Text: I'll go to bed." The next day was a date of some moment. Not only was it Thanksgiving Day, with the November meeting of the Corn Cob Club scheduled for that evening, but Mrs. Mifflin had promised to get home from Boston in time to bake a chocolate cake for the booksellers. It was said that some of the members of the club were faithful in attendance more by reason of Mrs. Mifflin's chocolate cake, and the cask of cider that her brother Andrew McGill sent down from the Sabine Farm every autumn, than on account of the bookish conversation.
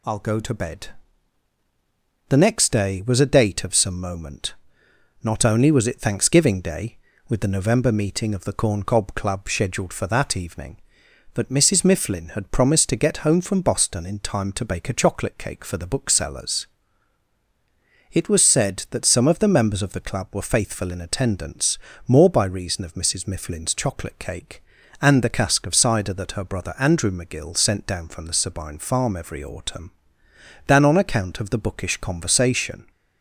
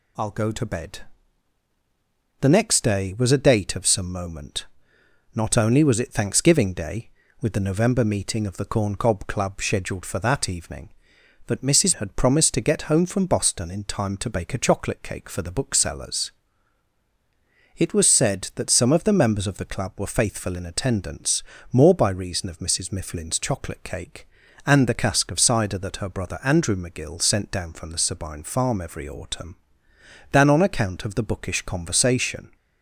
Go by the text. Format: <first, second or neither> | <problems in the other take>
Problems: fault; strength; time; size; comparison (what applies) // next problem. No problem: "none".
first | skips "Mifflin"; at 11.9 s // pauses between "attendance" and "more"; slight; at 21.4 s; 0.28 s long; slight in the first